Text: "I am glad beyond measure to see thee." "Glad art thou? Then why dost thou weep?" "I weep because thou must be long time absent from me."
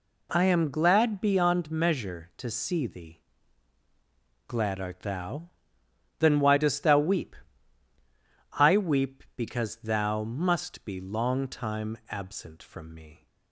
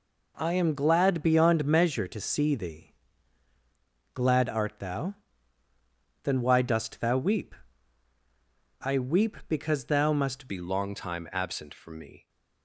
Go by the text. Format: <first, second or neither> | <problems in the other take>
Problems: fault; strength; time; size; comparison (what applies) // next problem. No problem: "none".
first | changes voice at "be"; from 10.4 s on; 1.8 s long